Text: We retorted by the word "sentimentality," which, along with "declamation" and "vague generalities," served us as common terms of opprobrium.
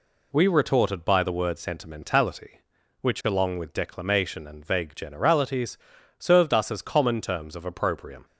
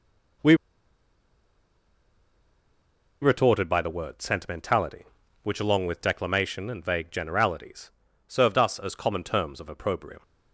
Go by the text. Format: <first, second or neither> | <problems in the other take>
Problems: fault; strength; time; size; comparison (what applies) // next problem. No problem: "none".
first | pauses between "We" and "retorted"; strong; at 0.5 s; 2.6 s long